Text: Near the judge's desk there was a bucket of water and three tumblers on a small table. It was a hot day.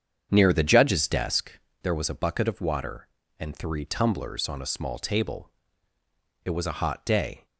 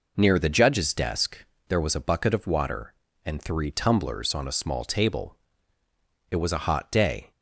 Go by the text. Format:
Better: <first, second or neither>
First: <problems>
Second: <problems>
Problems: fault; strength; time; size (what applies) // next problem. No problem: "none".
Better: second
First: starts louder than the rest; strong; until 1.5 s; 7.5 dB // pauses between "desk" and "there"; slight; at 1.5 s; 0.32 s long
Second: pauses between "desk" and "there"; slight; at 1.3 s; 0.32 s long